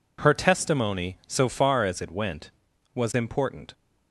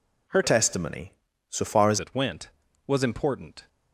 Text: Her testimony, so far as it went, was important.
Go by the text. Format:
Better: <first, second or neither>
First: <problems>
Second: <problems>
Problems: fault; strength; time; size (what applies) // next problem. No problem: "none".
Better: first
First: none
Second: changes voice from "testimony" to "as"; from 0.4 to 1.9 s; 1.5 s long